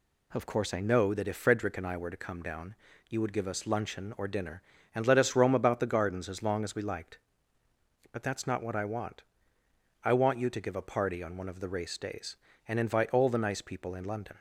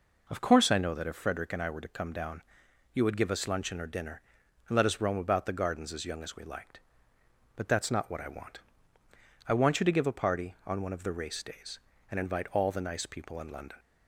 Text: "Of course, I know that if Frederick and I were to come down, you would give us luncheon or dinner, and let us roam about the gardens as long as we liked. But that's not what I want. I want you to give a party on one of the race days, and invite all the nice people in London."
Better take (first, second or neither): first